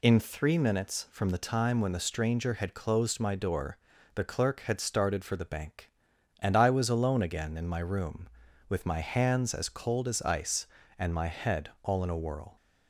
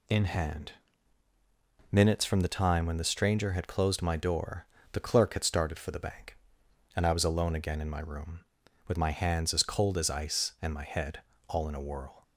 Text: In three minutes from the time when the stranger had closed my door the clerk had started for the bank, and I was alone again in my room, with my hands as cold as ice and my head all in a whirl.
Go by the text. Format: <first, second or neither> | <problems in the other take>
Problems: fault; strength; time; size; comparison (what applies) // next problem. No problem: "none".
first | says "hand" for "three"; at 0.2 s // pauses between "door" and "the"; slight; at 4.6 s; 0.28 s long; slight in the first // pauses between "head" and "all"; slight; at 11.2 s; 0.26 s long